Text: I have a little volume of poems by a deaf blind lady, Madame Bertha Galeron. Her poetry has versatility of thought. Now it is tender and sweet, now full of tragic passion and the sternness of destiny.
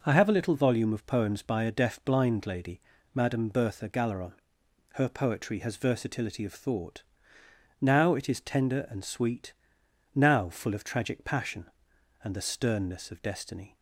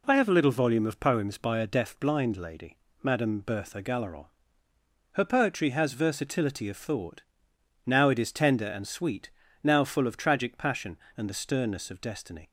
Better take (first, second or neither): neither